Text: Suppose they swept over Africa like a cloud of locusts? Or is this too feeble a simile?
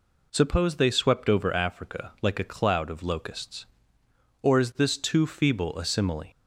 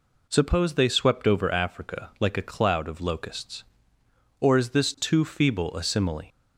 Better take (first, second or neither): neither